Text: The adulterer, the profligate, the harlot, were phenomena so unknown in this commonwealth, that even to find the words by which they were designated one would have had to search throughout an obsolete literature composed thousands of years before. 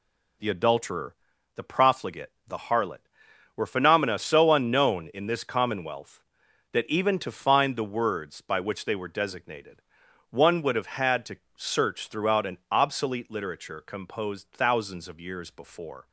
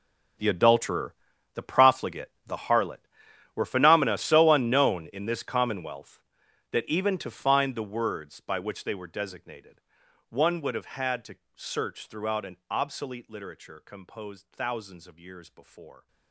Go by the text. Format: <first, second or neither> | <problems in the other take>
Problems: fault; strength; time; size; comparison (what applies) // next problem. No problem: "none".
first | gets quieter; strong; throughout; 17.5 dB // pauses between "designated" and "one"; noticeable; at 9.7 s; 0.50 s long; noticeable in the first // pauses between "to" and "search"; slight; at 11.3 s; 0.18 s long; slight in the first